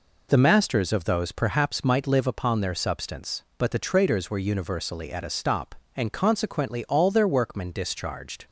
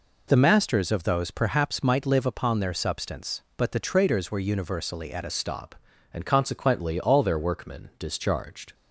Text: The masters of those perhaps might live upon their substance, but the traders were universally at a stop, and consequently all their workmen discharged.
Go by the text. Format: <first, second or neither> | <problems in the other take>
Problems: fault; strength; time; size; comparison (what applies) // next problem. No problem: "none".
first | changes voice at "stop"; from 5.2 s on; 3.5 s long